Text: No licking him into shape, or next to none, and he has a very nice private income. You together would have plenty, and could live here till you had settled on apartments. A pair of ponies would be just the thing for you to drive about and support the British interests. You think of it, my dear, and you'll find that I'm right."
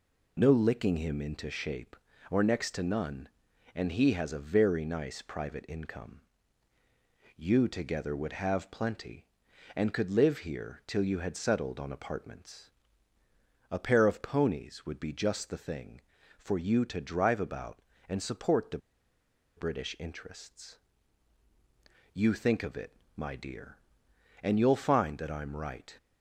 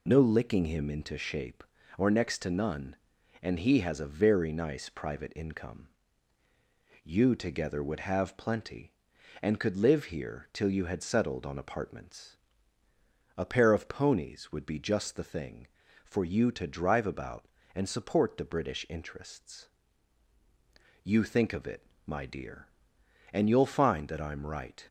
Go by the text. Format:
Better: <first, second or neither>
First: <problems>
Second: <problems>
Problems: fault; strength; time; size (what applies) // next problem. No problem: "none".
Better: second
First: pauses between "the" and "British"; noticeable; at 18.7 s; 0.78 s long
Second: none